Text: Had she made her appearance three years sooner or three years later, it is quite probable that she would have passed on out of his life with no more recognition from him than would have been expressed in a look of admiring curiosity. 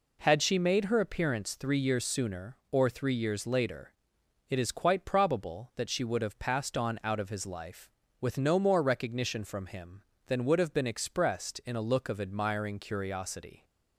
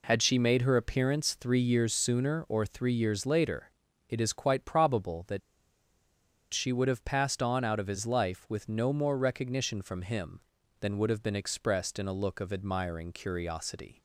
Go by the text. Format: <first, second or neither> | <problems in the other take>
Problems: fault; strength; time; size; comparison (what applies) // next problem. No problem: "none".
first | pauses between "that" and "she"; at 5.4 s; 1.1 s long